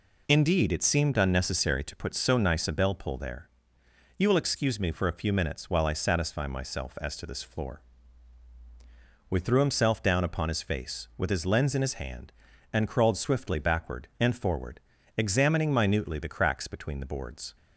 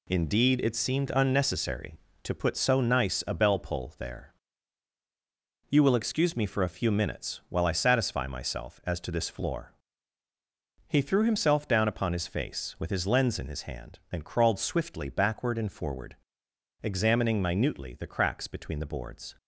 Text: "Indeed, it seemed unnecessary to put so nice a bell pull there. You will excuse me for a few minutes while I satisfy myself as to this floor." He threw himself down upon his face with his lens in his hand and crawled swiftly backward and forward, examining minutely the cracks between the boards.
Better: second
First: says "We" for "He"; at 9.2 s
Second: none

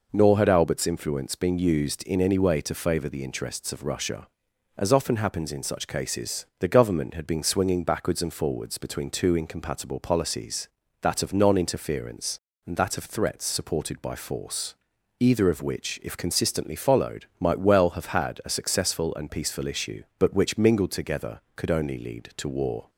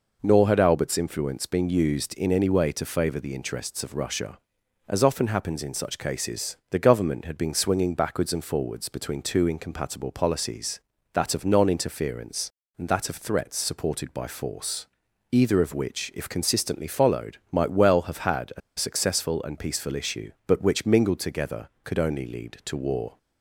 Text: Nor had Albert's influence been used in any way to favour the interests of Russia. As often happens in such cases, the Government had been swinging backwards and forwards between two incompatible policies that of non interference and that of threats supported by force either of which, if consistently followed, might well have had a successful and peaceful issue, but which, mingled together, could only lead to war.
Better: first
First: pauses between "force" and "either"; noticeable; at 14.7 s; 0.46 s long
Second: pauses between "force" and "either"; noticeable; at 14.8 s; 0.46 s long // pauses between "a" and "successful"; slight; at 18.6 s; 0.17 s long

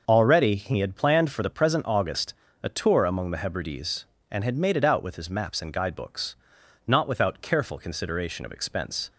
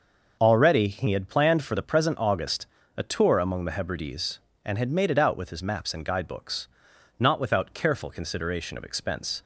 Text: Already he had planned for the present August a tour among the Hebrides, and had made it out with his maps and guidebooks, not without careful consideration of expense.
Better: neither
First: starts louder than the rest; noticeable; until 1.0 s; 6 dB // pauses between "August" and "a"; slight; at 2.3 s; 0.26 s long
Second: starts louder than the rest; noticeable; until 1.4 s; 6 dB // pauses between "August" and "a"; slight; at 2.6 s; 0.28 s long

